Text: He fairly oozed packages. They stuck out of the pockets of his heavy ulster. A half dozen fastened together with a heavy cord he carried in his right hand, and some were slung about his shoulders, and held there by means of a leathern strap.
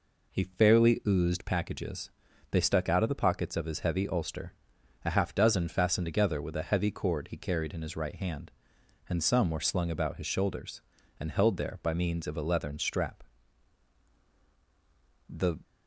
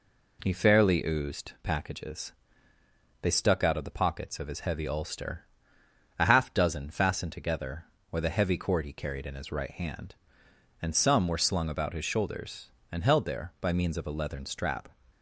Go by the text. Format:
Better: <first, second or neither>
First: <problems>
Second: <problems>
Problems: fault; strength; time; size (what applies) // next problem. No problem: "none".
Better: second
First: goes on to say "The"; slight; from 15.2 s on; 0.30 s long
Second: none